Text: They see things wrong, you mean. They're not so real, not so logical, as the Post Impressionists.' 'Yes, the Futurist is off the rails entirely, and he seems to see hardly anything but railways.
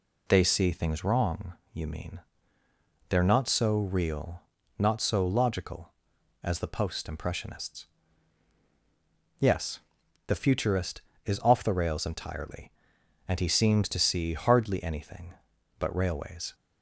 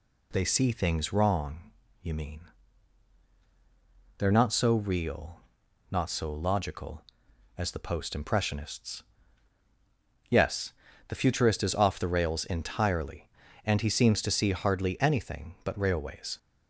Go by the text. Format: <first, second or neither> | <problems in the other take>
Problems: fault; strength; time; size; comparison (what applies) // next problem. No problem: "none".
neither | none